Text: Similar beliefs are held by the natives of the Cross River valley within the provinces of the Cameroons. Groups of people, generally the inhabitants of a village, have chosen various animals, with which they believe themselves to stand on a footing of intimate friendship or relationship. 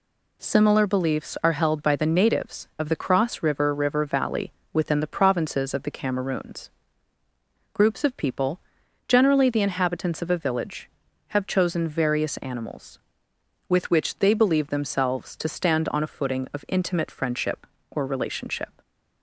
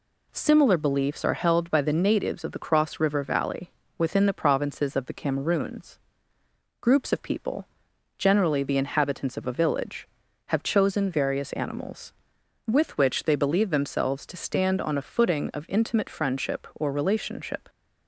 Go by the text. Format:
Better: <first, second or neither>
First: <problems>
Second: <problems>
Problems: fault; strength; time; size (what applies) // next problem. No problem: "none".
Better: second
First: says "River" twice; at 3.7 s // pauses between "valley" and "within"; slight; at 4.5 s; 0.20 s long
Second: pauses between "valley" and "within"; slight; at 3.7 s; 0.26 s long